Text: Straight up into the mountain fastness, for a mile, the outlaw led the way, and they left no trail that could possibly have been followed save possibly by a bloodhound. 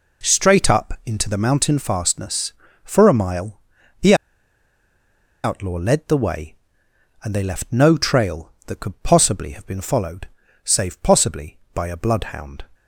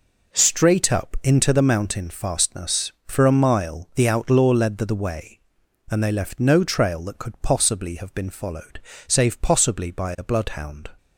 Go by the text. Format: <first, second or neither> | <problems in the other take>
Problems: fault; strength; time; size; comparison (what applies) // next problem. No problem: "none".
second | pauses between "the" and "outlaw"; strong; at 4.1 s; 1.3 s long // pauses between "followed" and "save"; slight; at 10.2 s; 0.36 s long; slight in the second